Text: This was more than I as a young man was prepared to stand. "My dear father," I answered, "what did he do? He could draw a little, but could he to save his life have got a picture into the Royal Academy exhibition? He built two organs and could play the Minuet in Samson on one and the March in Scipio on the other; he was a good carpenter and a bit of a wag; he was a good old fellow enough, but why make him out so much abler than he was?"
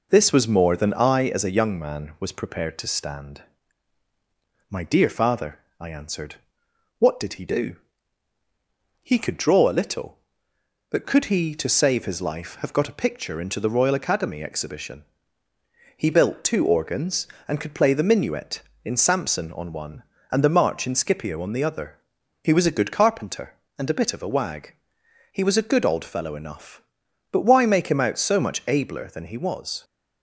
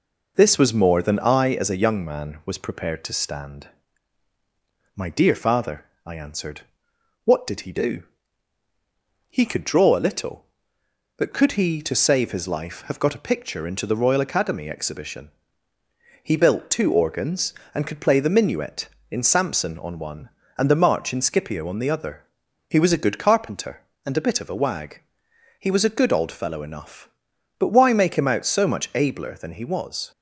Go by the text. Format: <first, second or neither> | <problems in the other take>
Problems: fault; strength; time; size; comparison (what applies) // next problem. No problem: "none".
neither | none